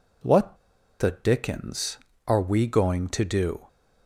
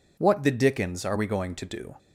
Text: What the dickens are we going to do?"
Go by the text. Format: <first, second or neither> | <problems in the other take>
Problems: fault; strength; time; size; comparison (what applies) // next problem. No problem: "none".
second | pauses between "What" and "the"; at 0.5 s; 0.42 s long